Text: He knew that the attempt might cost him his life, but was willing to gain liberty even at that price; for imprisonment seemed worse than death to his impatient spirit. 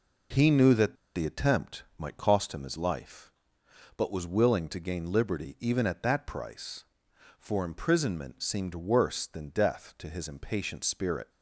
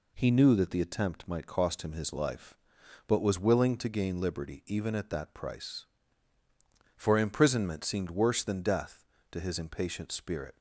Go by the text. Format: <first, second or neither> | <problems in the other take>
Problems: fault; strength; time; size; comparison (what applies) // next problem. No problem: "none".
second | pauses between "that" and "the"; slight; at 0.9 s; 0.19 s long